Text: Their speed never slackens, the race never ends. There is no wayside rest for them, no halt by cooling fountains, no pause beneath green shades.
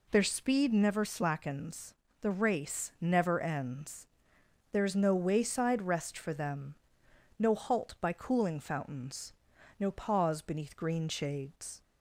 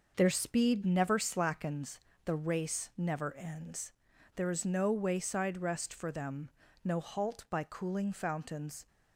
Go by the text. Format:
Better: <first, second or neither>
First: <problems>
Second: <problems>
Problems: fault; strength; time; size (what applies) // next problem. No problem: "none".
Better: first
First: none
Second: stops before "no pause beneath green shades"; at 8.8 s